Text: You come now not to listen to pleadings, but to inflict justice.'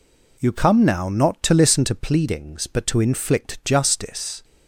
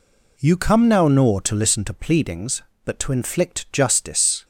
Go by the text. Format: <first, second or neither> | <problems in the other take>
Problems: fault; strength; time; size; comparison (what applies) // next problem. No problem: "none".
first | says "nor" for "not"; at 1.0 s